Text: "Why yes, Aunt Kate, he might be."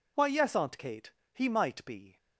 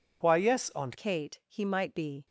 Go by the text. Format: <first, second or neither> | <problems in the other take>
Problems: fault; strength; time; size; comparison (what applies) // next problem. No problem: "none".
first | changes voice at "Kate"; from 0.9 s on; 1.3 s long